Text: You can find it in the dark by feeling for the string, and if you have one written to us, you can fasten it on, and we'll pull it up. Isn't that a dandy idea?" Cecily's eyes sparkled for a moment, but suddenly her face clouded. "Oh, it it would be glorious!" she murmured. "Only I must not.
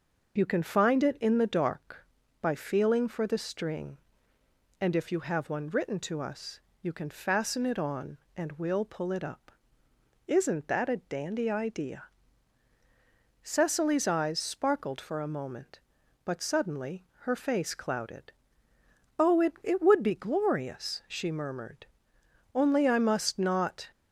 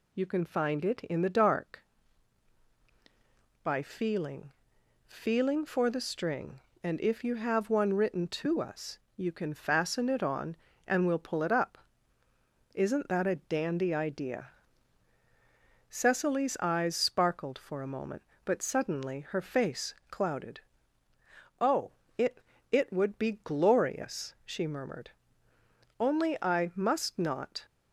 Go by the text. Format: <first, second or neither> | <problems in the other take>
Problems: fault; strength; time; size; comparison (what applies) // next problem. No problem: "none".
first | says "feeling" twice; at 5.0 s // pauses between "face" and "clouded"; slight; at 19.9 s; 0.16 s long // pauses between "it" and "it"; slight; at 22.3 s; 0.30 s long